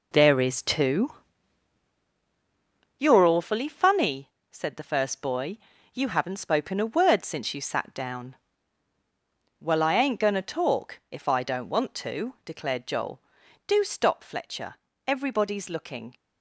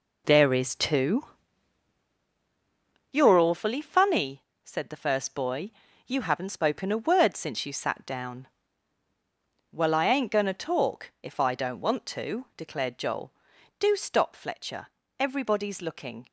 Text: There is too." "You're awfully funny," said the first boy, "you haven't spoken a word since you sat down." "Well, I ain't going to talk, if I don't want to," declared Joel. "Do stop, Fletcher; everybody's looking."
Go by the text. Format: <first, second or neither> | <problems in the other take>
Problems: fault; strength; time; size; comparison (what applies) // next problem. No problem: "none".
neither | none